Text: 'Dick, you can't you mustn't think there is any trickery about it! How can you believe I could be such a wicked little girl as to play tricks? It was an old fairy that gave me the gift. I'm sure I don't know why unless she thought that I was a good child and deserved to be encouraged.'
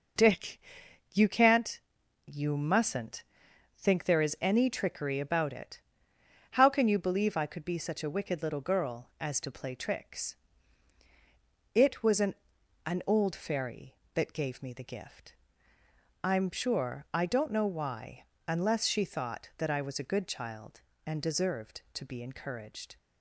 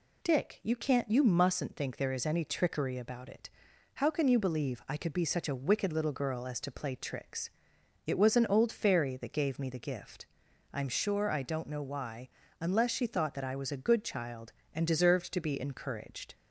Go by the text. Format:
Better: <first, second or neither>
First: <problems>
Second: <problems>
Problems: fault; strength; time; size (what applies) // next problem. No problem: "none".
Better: second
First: pauses between "can't" and "you"; noticeable; at 1.7 s; 0.46 s long // pauses between "mustn't" and "think"; noticeable; at 3.2 s; 0.54 s long // says "an" twice; at 12.8 s // pauses between "why" and "unless"; slight; at 18.2 s; 0.24 s long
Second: pauses between "why" and "unless"; slight; at 12.2 s; 0.32 s long